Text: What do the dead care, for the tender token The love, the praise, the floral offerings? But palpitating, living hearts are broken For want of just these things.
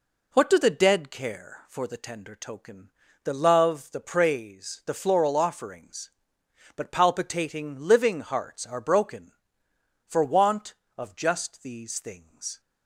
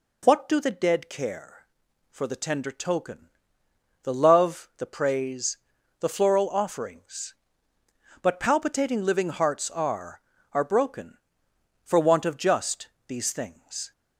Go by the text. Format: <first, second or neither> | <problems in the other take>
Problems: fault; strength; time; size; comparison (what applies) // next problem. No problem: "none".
first | pauses between "token" and "The"; noticeable; at 3.2 s; 0.76 s long; slight in the first // says "are" twice; at 10.5 s // pauses between "just" and "these"; slight; at 12.8 s; 0.22 s long